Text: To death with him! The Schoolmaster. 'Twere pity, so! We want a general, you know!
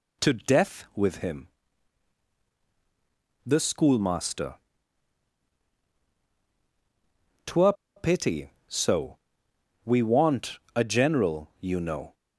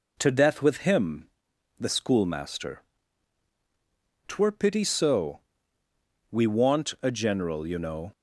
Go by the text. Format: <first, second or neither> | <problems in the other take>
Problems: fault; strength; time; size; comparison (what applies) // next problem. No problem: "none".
second | pauses between "Twere" and "pity"; slight; at 7.7 s; 0.23 s long